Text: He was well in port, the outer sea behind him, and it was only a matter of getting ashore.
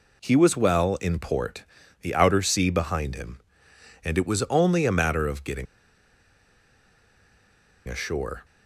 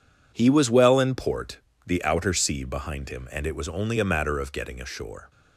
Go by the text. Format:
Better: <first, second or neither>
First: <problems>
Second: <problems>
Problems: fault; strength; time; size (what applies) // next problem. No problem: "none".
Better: second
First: pauses between "getting" and "ashore"; strong; at 5.6 s; 2.2 s long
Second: none